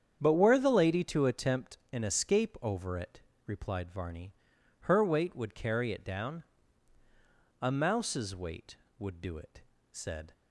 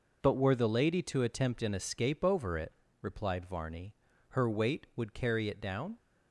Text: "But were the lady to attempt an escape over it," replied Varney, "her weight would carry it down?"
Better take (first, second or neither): second